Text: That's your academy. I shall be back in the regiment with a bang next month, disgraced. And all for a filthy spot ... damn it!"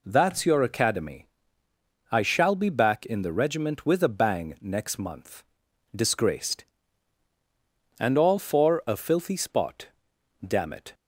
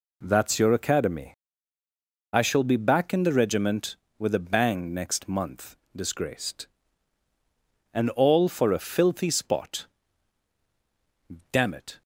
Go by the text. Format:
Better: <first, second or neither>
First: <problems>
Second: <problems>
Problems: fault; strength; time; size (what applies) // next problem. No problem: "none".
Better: neither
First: none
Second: none